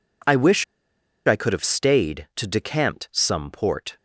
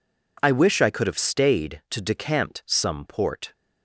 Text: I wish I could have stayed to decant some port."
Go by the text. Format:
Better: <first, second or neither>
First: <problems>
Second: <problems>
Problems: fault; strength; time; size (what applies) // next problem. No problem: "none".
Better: second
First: pauses between "wish" and "I"; noticeable; at 0.6 s; 0.61 s long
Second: none